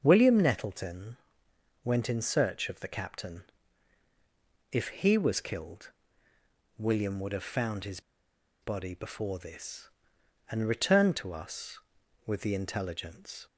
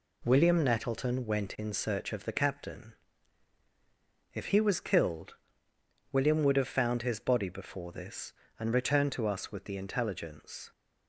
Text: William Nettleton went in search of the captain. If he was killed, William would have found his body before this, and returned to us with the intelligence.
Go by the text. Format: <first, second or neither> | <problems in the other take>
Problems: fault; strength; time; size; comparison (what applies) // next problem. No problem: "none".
second | starts louder than the rest; until 1.0 s; 6 dB // pauses between "Nettleton" and "went"; noticeable; at 1.1 s; 0.68 s long // pauses between "his" and "body"; noticeable; at 7.9 s; 0.62 s long